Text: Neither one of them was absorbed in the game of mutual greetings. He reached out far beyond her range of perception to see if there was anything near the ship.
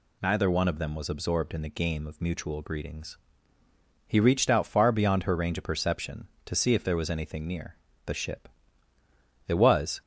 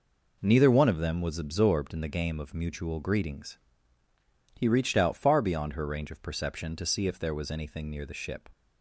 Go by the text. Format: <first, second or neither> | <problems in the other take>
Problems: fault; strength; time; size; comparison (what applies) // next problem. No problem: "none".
second | pauses between "near" and "the"; slight; at 7.7 s; 0.30 s long // goes on to say "It was"; from 9.4 s on; 0.54 s long